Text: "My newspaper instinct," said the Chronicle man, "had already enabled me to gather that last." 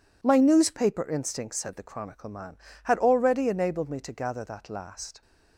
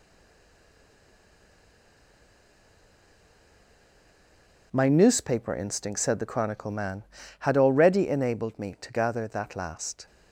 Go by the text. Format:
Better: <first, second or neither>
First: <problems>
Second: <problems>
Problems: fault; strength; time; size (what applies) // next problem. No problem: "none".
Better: first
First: none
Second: stays silent before the first word; strong; until 4.7 s; 4.7 s long